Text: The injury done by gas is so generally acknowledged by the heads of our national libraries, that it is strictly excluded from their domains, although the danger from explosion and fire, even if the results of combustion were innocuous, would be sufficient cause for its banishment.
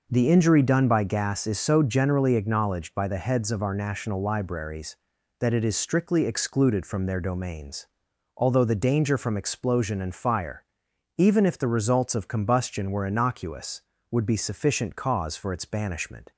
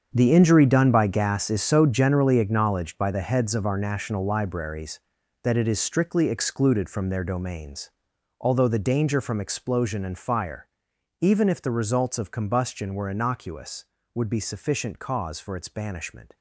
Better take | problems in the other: first | gets quieter; strong; throughout; 13.5 dB

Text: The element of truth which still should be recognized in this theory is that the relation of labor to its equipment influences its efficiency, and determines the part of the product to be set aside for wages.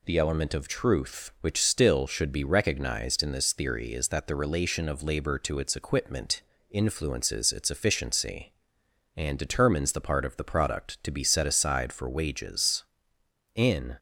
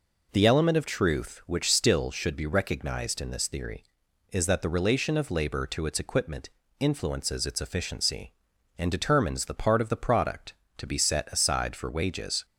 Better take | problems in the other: second | pauses between "equipment" and "influences"; slight; at 6.4 s; 0.28 s long; slight in the second // goes on to say "In"; slight; from 13.5 s on; 0.42 s long

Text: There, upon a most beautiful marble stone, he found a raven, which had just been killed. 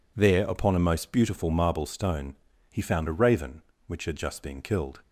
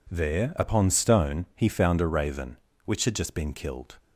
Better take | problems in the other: first | skips "a most beautiful marble"; at 0.8 s

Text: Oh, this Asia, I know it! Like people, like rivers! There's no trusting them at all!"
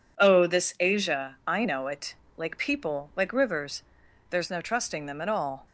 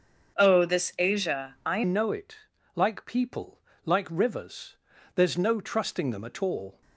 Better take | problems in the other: first | starts louder than the rest; until 1.4 s; 6.5 dB // changes voice at "know"; from 1.8 s on; 5.0 s long

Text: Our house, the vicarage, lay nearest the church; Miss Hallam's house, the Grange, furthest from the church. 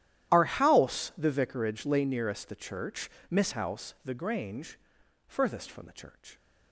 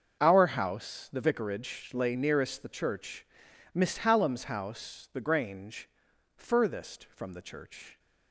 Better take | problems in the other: second | starts louder than the rest; strong; until 1.3 s; 12 dB; also in the second // skips "Hallam's"; at 3.5 s

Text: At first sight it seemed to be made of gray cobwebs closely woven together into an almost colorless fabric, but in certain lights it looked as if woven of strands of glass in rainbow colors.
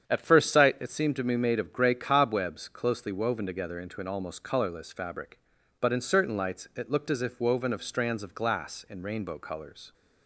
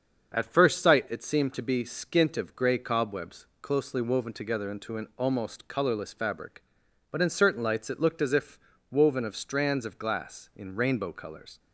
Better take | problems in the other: first | starts louder than the rest; until 1.4 s; 7 dB; strong in the first // says "skint" for "made"; at 1.8 s // pauses between "cobwebs" and "closely"; slight; at 3.4 s; 0.16 s long // pauses between "if" and "woven"; slight; at 8.5 s; 0.30 s long

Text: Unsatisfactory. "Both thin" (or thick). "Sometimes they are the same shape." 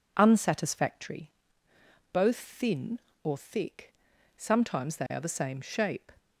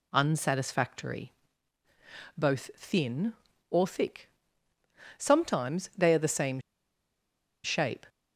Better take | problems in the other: first | pauses between "same" and "shape"; at 6.5 s; 1.0 s long

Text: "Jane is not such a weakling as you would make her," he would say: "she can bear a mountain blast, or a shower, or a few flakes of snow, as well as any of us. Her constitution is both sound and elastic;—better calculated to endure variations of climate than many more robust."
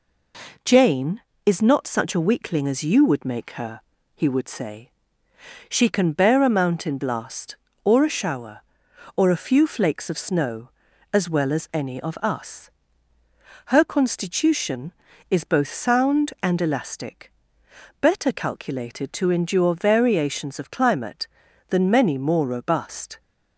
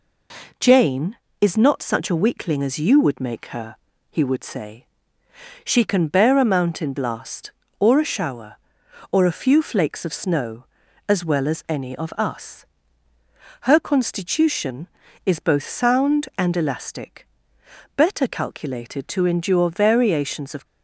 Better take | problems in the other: first | stops before "climate than many more robust"; at 20.6 s

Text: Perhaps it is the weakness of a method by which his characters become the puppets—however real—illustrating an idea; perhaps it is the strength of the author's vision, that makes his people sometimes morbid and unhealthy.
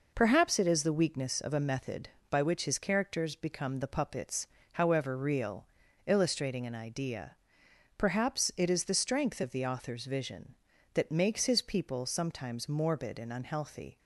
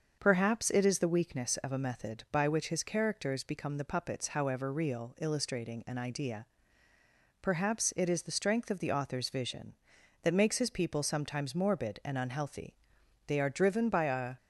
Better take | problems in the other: first | starts louder than the rest; until 1.2 s; 6.5 dB // goes on to say "They are driven by a"; noticeable; from 13.2 s on; 1.0 s long

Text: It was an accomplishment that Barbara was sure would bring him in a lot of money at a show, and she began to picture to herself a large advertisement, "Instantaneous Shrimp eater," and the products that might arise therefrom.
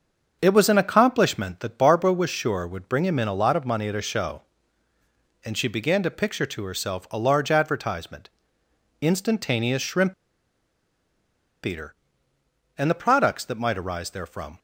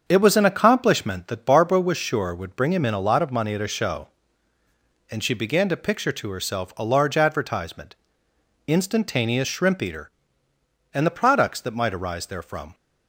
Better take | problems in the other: second | starts louder than the rest; until 1.4 s; 6.5 dB; also in the second // pauses between "Shrimp" and "eater"; strong; at 10.1 s; 1.5 s long

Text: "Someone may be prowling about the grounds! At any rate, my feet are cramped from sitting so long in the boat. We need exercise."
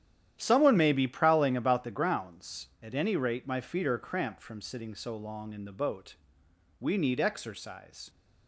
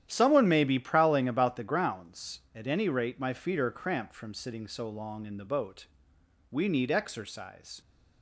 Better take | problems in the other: neither | starts louder than the rest; strong; the same in both

